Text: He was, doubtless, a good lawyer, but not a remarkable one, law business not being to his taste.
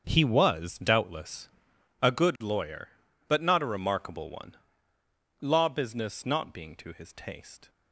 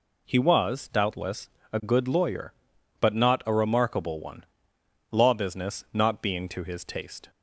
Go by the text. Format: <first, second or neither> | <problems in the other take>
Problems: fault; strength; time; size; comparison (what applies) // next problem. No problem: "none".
second | gets quieter; strong; throughout; 13 dB